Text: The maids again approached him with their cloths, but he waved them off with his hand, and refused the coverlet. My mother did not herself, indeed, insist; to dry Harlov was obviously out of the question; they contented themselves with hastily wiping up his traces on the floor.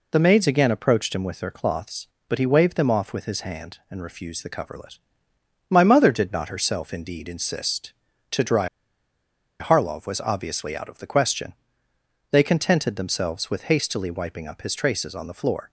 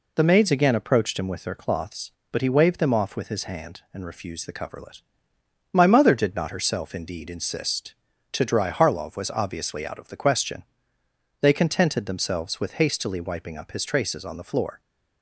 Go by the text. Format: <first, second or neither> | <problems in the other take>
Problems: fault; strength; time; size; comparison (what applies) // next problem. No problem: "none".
second | pauses between "dry" and "Harlov"; noticeable; at 8.6 s; 0.91 s long